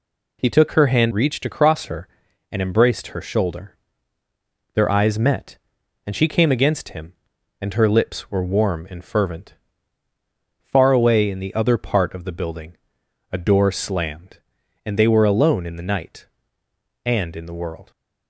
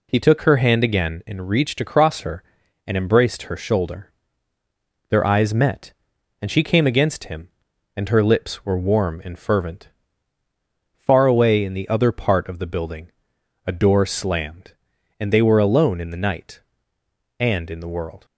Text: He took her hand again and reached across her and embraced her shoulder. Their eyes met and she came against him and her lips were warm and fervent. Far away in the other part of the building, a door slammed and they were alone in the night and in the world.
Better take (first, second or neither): second